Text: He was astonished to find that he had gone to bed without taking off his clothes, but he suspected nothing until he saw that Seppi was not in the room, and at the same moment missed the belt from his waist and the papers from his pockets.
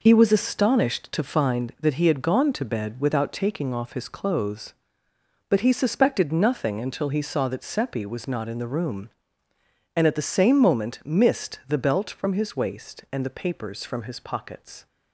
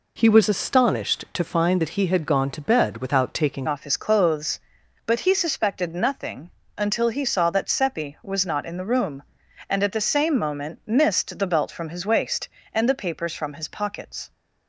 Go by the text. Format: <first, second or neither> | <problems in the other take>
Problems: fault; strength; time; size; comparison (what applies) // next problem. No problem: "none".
first | changes voice at "off"; from 3.6 s on; 10.7 s long // pauses between "nothing" and "until"; slight; at 6.5 s; 0.26 s long